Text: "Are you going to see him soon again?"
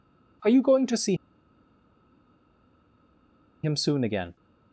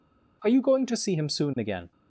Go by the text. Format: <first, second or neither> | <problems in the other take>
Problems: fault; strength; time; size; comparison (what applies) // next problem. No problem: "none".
second | pauses between "see" and "him"; strong; at 1.1 s; 2.4 s long